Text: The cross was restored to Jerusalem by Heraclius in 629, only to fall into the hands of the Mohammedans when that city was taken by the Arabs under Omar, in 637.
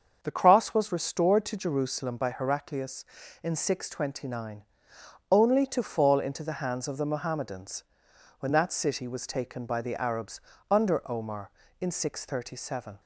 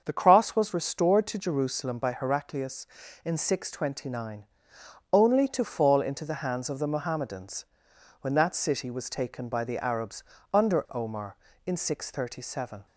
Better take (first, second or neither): neither